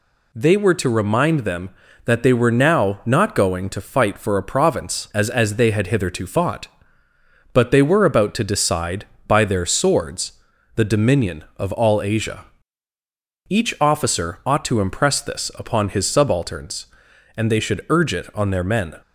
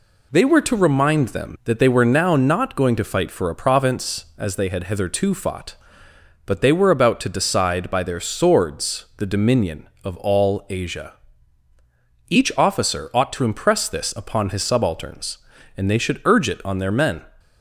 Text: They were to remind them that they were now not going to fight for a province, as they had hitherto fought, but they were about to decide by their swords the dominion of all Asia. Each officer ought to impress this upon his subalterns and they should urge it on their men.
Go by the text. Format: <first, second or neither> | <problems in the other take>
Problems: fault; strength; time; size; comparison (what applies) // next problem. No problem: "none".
second | says "as" twice; at 5.2 s // pauses between "swords" and "the"; at 10.3 s; 0.44 s long